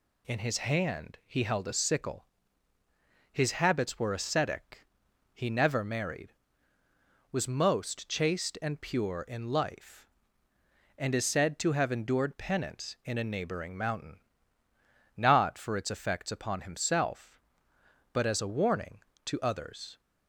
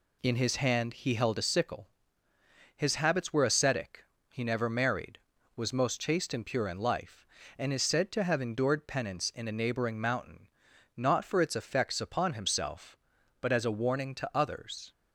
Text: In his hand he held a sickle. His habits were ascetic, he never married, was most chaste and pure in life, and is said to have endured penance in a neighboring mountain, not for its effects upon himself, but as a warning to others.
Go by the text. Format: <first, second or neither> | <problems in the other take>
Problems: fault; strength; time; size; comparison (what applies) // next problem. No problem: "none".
neither | none